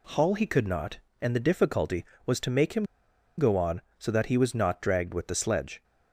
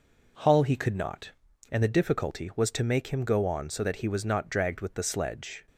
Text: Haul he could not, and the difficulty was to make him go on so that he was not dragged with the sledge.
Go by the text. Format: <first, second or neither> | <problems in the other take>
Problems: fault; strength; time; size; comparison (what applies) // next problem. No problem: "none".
second | pauses between "him" and "go"; noticeable; at 2.8 s; 0.54 s long